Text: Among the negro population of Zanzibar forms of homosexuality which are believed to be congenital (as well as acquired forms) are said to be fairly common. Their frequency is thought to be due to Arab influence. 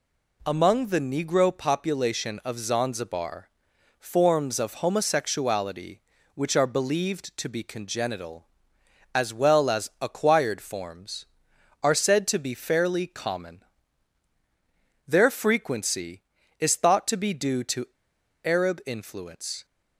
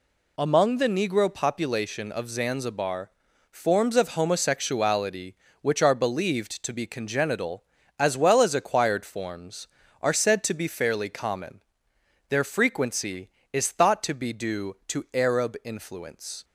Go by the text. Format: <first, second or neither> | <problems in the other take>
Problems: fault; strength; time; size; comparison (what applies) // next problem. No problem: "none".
second | pauses between "Zanzibar" and "forms"; noticeable; at 3.4 s; 0.50 s long; also in the second // pauses between "to" and "Arab"; noticeable; at 17.8 s; 0.56 s long